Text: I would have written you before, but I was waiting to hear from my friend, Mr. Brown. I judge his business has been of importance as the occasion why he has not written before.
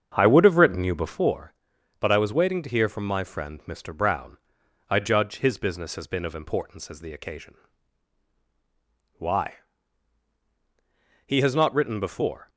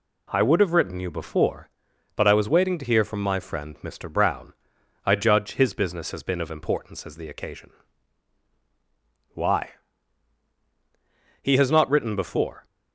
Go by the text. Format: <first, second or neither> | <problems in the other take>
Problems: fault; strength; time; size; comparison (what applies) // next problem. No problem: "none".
second | starts louder than the rest; strong; until 1.2 s; 7.5 dB // pauses between "occasion" and "why"; strong; at 7.5 s; 1.6 s long; strong in the second // pauses between "why" and "he"; strong; at 9.5 s; 1.7 s long; strong in the second